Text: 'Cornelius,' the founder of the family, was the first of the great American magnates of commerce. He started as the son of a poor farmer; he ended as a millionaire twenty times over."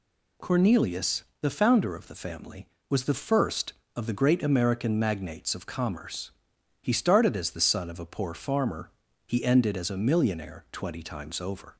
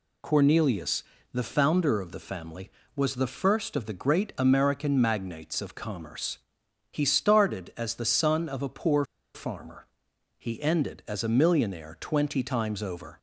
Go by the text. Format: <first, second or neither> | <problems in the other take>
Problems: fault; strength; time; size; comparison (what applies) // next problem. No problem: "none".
first | pauses between "poor" and "farmer"; slight; at 9.0 s; 0.29 s long